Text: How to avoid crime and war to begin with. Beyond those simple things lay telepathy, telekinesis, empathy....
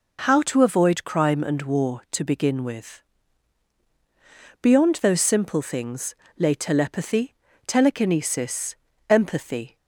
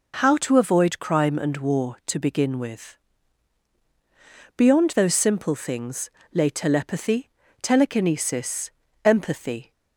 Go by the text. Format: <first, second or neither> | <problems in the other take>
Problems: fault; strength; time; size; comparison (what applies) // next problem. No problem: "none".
neither | pauses between "things" and "lay"; slight; the same in both